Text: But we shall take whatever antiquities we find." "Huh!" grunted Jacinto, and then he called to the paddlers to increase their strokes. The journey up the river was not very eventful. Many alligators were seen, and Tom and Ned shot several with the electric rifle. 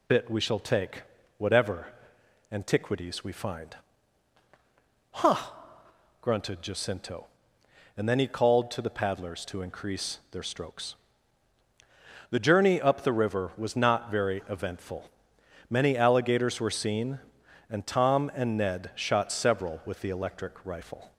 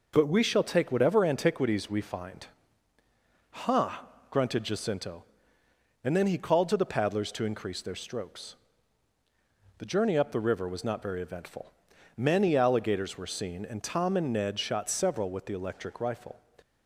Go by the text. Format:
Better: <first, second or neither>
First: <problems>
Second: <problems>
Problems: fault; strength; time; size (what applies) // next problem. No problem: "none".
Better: second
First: says "Bit" for "But"; at 0.0 s // pauses between "take" and "whatever"; slight; at 1.0 s; 0.34 s long // pauses between "whatever" and "antiquities"; noticeable; at 1.8 s; 0.64 s long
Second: none